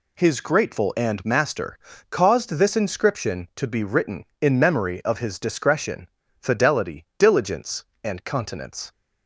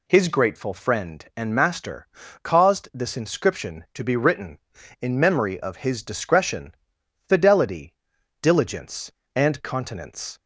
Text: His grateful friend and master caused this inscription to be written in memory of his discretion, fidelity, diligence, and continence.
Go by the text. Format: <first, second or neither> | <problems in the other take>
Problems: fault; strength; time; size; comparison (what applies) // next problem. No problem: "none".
second | skips "friend"; at 0.9 s // pauses between "master" and "caused"; slight; at 1.7 s; 0.32 s long; also in the second